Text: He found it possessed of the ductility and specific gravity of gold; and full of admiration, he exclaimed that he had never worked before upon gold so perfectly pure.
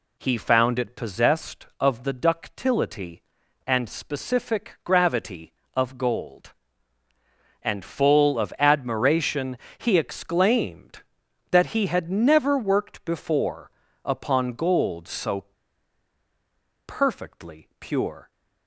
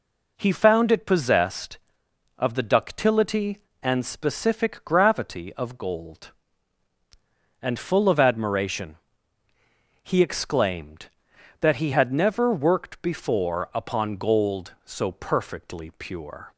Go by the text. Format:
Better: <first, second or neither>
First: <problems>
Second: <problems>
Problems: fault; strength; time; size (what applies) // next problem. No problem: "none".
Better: second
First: pauses between "before" and "upon"; slight; at 13.7 s; 0.34 s long // pauses between "so" and "perfectly"; strong; at 15.4 s; 1.4 s long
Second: none